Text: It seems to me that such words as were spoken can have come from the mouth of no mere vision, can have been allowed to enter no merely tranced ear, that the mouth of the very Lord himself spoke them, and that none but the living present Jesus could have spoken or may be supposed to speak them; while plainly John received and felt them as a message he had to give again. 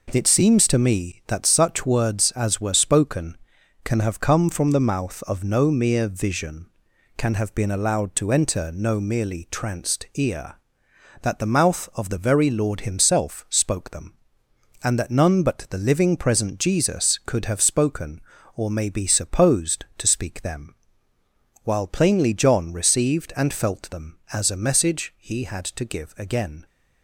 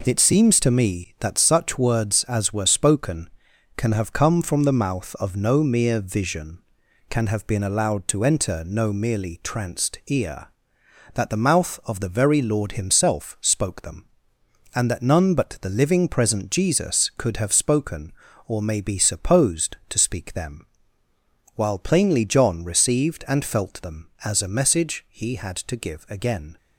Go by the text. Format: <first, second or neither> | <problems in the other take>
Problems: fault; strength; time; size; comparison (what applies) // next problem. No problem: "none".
neither | none